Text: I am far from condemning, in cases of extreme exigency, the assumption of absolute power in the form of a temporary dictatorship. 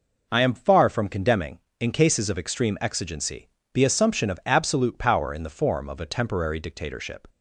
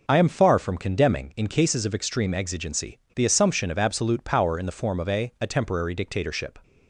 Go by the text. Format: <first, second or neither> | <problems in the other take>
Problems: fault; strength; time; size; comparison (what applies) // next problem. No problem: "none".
first | says "a" twice; at 5.4 s